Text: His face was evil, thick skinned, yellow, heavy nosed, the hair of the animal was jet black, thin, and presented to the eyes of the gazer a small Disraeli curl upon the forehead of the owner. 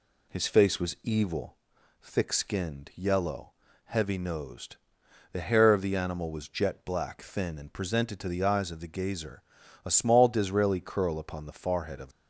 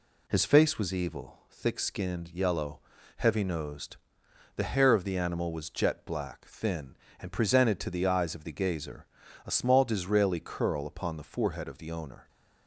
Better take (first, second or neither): second